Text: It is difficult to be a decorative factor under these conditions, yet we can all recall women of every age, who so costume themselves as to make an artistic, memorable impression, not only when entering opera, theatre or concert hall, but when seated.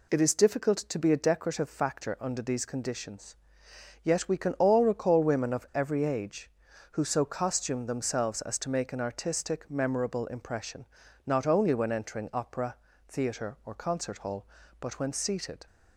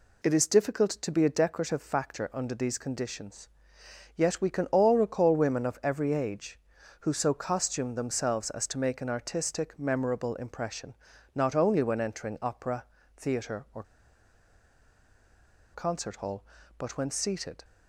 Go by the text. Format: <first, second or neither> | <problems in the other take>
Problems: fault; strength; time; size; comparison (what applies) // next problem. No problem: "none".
first | pauses between "or" and "concert"; strong; at 13.8 s; 1.9 s long